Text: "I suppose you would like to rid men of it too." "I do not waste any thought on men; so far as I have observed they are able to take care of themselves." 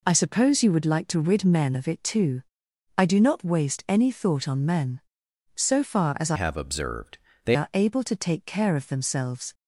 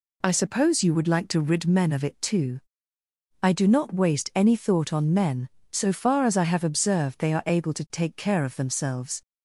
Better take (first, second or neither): second